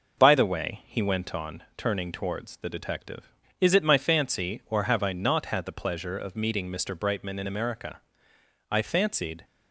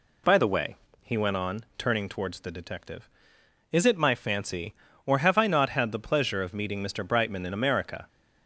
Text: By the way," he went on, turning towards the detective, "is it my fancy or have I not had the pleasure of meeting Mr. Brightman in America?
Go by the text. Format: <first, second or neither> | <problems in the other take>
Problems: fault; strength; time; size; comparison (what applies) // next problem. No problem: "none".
second | goes on to say "I fancied"; noticeable; from 8.7 s on; 0.74 s long